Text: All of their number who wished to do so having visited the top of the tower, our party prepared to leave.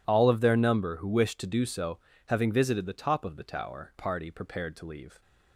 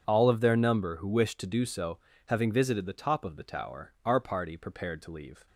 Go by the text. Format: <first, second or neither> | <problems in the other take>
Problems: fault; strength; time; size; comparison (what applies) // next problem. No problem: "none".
second | pauses between "so" and "having"; slight; at 1.9 s; 0.30 s long; slight in the second // skips "our"; at 3.9 s